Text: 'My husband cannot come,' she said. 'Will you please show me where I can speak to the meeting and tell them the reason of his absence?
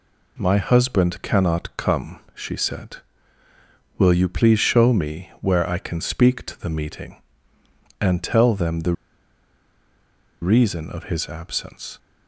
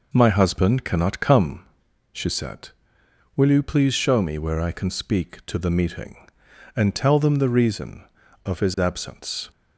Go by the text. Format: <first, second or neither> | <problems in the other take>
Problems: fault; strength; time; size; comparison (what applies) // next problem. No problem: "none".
second | pauses between "the" and "reason"; strong; at 8.9 s; 1.4 s long